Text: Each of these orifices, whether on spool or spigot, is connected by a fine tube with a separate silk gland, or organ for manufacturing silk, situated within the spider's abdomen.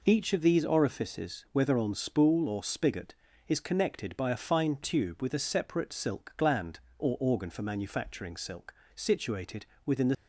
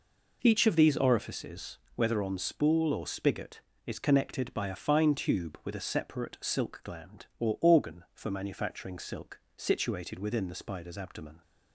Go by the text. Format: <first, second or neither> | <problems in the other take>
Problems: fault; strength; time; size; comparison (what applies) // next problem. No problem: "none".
second | pauses between "situated" and "within"; slight; at 9.6 s; 0.22 s long // stops before "spider's abdomen"; at 10.1 s